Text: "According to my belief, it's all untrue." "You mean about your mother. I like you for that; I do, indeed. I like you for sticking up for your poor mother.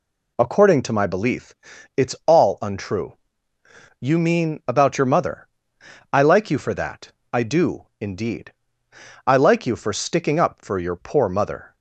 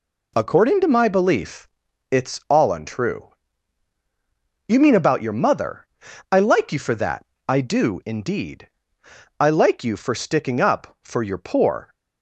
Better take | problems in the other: first | stops before "mother"; at 11.9 s

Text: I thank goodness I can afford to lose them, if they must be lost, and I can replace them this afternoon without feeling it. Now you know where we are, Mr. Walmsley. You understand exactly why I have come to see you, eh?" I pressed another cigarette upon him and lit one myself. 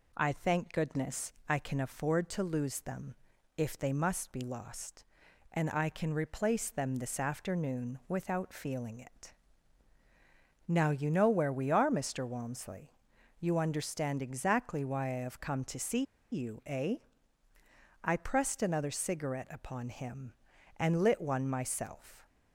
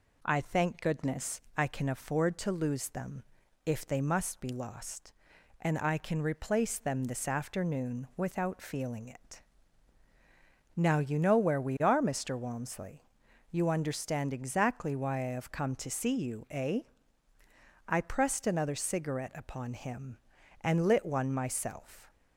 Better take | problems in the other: second | pauses between "goodness" and "I"; slight; at 1.3 s; 0.16 s long; slight in the second // pauses between "see" and "you"; slight; at 16.0 s; 0.28 s long

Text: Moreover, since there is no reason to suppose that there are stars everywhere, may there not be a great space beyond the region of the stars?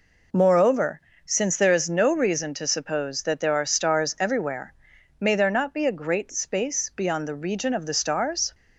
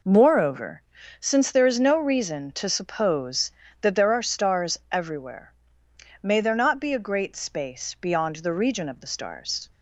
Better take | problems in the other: neither | none

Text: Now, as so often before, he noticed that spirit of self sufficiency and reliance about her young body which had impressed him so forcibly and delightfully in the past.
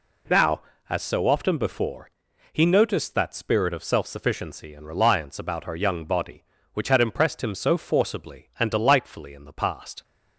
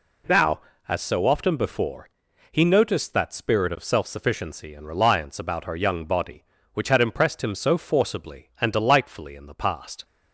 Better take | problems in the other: neither | none

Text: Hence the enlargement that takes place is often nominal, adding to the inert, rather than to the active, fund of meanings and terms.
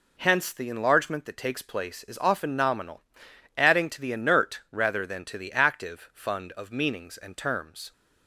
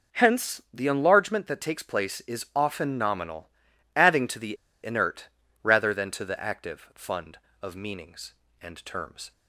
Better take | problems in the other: first | pauses between "the" and "inert"; slight; at 4.5 s; 0.27 s long

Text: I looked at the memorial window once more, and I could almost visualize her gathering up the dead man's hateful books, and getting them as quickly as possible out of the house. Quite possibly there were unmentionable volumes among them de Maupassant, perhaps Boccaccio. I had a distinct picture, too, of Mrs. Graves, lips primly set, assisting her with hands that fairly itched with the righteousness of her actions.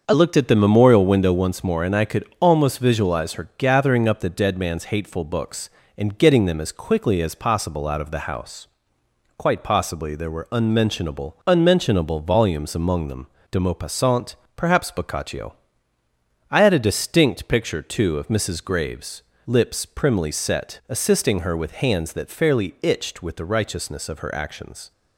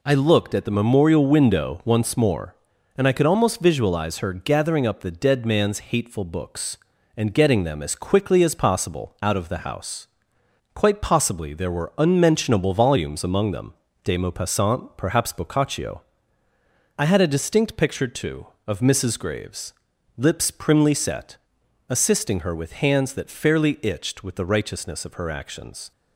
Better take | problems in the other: second | starts louder than the rest; until 1.0 s; 6.5 dB // says "unmentionable" twice; at 11.4 s // pauses between "them" and "de"; slight; at 13.2 s; 0.24 s long; slight in the second

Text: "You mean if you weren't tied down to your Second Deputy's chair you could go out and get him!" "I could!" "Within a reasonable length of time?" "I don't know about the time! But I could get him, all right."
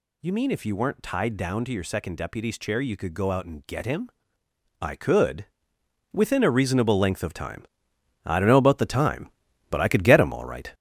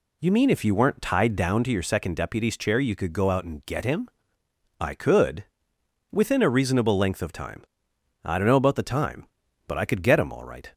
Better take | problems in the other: second | gets louder; noticeable; throughout; 6 dB

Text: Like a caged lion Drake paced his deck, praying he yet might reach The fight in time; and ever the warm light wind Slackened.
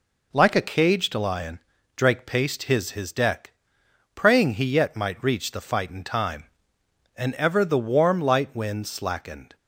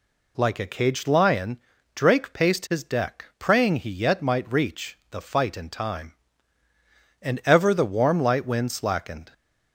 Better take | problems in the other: second | pauses between "lion" and "Drake"; slight; at 1.5 s; 0.36 s long; slight in the second // says "his" twice; at 2.9 s

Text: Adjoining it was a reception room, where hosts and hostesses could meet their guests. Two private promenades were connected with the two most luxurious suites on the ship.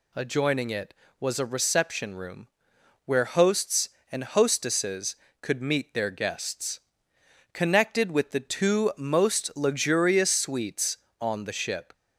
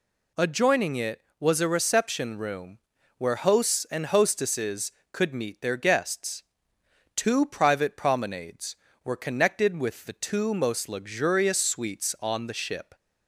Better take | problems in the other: second | skips "Two private promenades were"; at 7.1 s

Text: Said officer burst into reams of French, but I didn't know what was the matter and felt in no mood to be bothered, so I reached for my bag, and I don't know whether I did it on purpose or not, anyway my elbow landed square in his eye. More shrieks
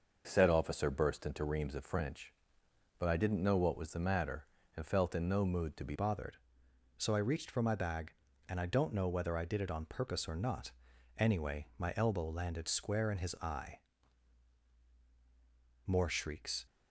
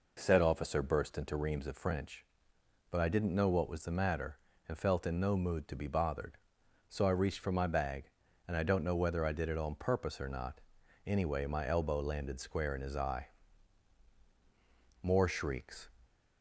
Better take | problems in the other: second | changes voice at "bothered"; from 5.9 s on; 10.7 s long

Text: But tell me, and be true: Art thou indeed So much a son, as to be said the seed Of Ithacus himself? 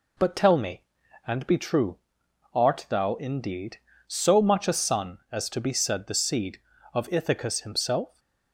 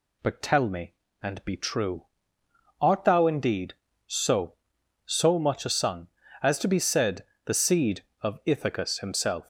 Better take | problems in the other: first | says "So" twice; at 5.0 s // pauses between "said" and "the"; slight; at 7.2 s; 0.22 s long

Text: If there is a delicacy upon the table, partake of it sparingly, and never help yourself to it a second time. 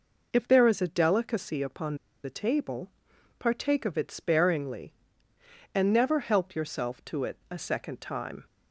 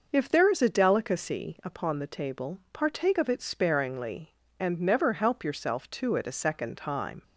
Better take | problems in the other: second | pauses between "upon" and "the"; slight; at 1.9 s; 0.27 s long

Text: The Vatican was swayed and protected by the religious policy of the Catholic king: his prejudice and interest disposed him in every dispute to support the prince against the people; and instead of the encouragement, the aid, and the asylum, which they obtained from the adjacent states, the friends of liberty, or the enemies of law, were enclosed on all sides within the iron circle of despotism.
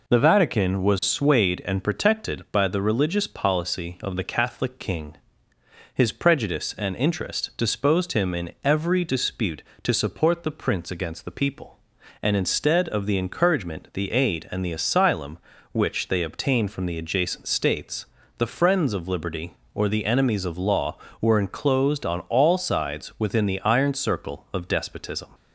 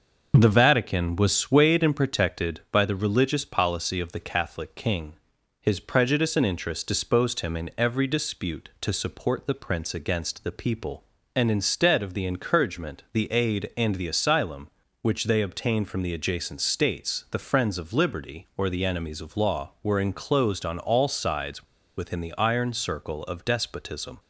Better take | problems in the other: first | pauses between "sides" and "within"; slight; at 21.6 s; 0.33 s long

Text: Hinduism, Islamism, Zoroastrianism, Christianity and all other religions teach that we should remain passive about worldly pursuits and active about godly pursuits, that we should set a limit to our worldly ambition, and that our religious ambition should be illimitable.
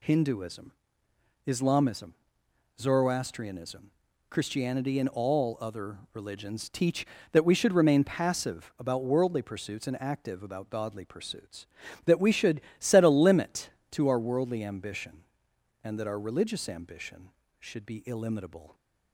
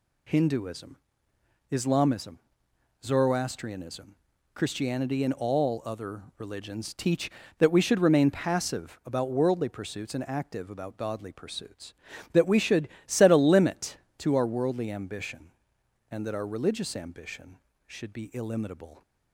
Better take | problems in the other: neither | pauses between "should" and "set"; slight; the same in both

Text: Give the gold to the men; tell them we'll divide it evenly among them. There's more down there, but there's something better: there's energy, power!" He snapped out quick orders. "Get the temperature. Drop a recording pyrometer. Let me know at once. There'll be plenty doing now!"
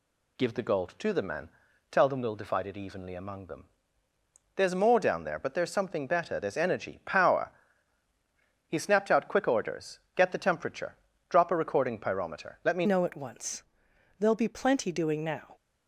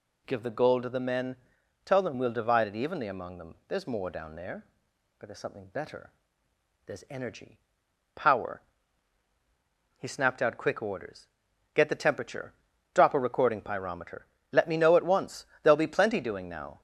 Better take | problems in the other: second | changes voice at "know"; from 12.8 s on; 2.7 s long

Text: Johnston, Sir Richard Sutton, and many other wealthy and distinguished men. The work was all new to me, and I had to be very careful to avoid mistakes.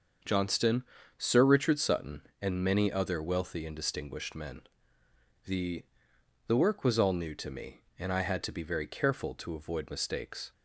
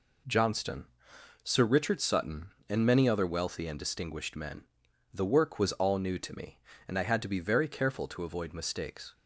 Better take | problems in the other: second | starts louder than the rest; until 1.5 s; 6.5 dB // says "The" twice; at 6.4 s

